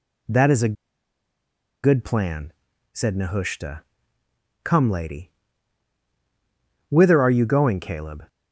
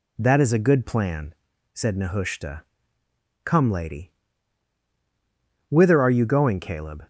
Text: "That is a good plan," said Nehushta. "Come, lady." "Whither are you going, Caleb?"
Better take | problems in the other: second | pauses between "a" and "good"; at 0.7 s; 1.0 s long

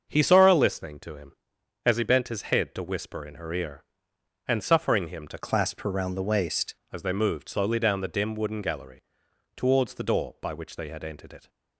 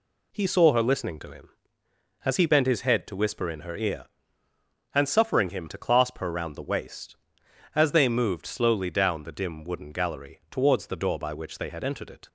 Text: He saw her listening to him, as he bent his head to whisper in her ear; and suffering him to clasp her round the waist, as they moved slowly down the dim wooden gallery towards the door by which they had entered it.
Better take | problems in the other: second | starts louder than the rest; until 1.1 s; 6.5 dB // changes voice from "clasp" to "waist"; from 5.3 to 6.7 s; 1.4 s long // pauses between "gallery" and "towards"; noticeable; at 9.0 s; 0.54 s long

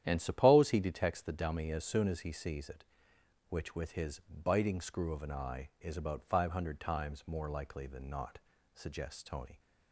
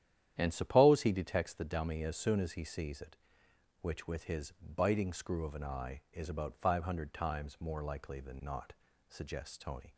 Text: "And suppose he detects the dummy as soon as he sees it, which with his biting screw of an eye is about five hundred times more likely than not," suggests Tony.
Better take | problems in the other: neither | starts louder than the rest; strong; the same in both

